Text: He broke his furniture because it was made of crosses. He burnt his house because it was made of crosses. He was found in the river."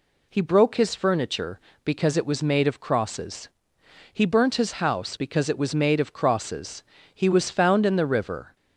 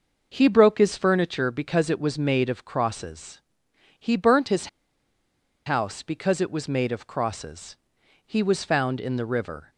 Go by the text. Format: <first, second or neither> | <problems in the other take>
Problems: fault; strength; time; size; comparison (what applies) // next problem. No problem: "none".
first | pauses between "his" and "house"; at 4.6 s; 0.99 s long